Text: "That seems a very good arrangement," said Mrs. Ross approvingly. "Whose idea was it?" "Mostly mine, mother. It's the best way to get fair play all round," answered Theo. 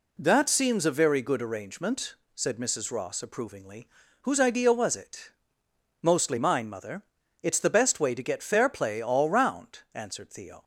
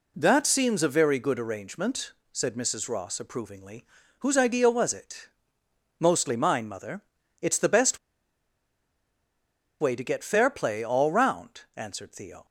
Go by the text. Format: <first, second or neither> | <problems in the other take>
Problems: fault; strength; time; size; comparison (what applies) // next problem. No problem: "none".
first | pauses between "best" and "way"; strong; at 7.9 s; 1.8 s long